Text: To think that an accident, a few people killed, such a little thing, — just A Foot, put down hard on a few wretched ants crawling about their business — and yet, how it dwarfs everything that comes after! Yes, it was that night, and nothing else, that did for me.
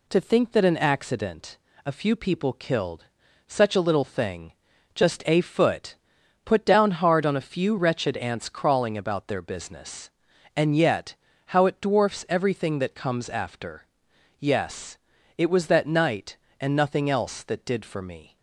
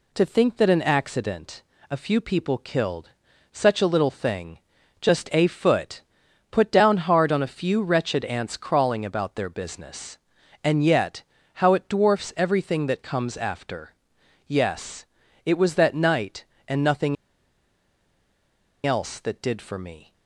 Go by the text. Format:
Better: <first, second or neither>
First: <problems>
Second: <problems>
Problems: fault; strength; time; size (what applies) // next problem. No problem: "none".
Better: first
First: none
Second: pauses between "nothing" and "else"; strong; at 17.1 s; 1.6 s long